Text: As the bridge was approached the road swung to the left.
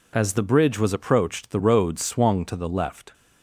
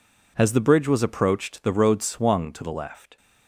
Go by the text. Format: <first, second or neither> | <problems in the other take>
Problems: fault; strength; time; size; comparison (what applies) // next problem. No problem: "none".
neither | none